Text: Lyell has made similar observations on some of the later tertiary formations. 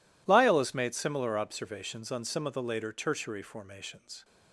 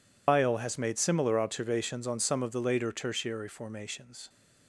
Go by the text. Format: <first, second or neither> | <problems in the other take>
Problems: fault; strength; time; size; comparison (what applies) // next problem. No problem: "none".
first | loses the start of "Lyell"; at 0.2 s; 140 ms